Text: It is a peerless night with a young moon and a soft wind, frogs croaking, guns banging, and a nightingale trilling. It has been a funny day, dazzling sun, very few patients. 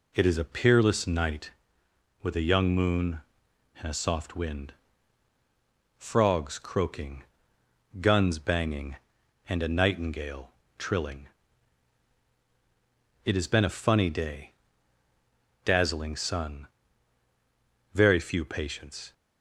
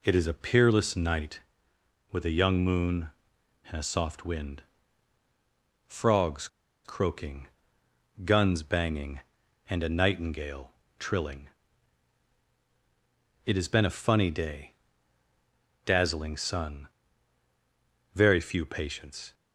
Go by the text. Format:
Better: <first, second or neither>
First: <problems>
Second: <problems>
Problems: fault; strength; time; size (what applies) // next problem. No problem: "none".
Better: first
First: pauses between "nightingale" and "trilling"; slight; at 10.5 s; 0.26 s long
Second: pauses between "frogs" and "croaking"; at 6.4 s; 0.37 s long // pauses between "nightingale" and "trilling"; slight; at 10.7 s; 0.26 s long